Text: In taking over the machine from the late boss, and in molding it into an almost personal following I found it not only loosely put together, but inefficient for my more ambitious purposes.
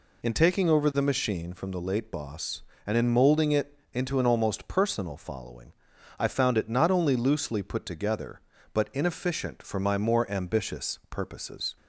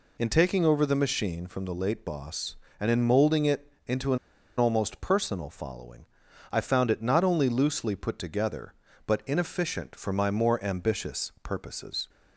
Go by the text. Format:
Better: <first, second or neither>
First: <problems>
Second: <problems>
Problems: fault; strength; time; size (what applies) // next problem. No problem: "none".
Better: first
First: pauses between "it" and "into"; slight; at 3.7 s; 0.16 s long // pauses between "following" and "I"; noticeable; at 5.7 s; 0.46 s long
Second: pauses between "it" and "into"; slight; at 3.7 s; 0.16 s long // pauses between "an" and "almost"; at 4.1 s; 0.40 s long // pauses between "following" and "I"; noticeable; at 6.0 s; 0.46 s long